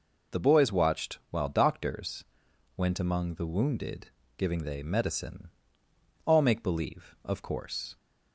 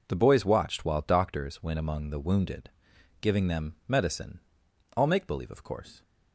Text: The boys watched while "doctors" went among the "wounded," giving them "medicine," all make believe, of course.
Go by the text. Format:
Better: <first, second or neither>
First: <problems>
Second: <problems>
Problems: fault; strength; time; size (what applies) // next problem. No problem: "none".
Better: second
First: pauses between "doctors" and "went"; noticeable; at 2.2 s; 0.50 s long // says "they" for "them"; at 4.6 s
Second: none